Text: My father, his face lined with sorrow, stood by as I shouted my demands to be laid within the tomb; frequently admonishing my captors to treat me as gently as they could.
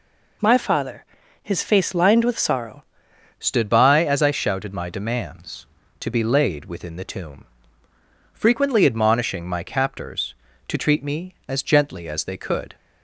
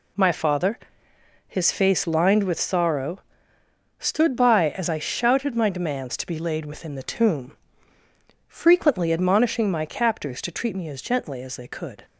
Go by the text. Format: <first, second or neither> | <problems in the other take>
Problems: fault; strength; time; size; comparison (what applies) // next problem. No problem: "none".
second | changes voice at "stood"; from 3.3 s on; 9.4 s long